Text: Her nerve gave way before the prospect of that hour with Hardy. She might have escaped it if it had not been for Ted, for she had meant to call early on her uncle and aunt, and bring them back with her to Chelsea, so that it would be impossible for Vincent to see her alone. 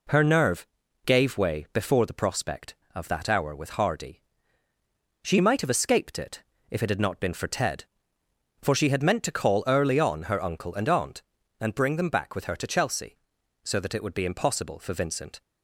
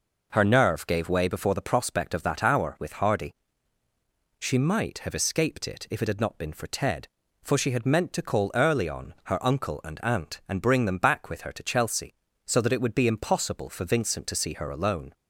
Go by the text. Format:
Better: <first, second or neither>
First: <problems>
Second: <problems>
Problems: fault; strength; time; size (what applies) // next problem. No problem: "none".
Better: second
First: pauses between "nerve" and "gave"; at 0.6 s; 0.38 s long // pauses between "it" and "if"; slight; at 6.4 s; 0.28 s long // stops before "to see her alone"; at 15.4 s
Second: none